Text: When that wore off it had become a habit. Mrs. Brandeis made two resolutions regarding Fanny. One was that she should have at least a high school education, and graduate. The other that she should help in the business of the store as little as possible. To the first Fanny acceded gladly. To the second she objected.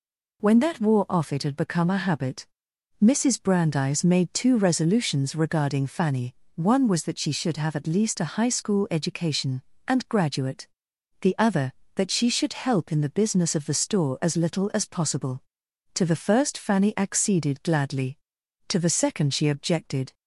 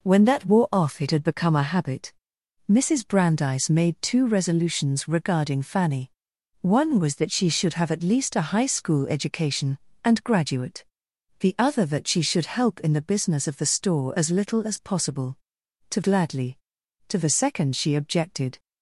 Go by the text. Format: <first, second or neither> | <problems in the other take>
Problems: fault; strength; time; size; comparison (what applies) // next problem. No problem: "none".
first | skips "the first Fanny acceded"; at 16.0 s